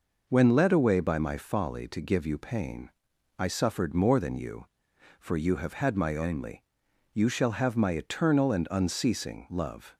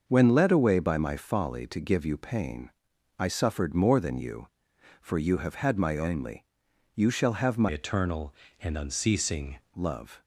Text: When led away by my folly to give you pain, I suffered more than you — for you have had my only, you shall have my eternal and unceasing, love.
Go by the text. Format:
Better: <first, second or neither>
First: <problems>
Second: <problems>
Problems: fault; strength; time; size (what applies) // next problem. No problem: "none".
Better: first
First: none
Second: starts louder than the rest; noticeable; until 1.0 s; 6 dB // changes voice from "eternal" to "unceasing"; from 7.6 to 9.5 s; 1.9 s long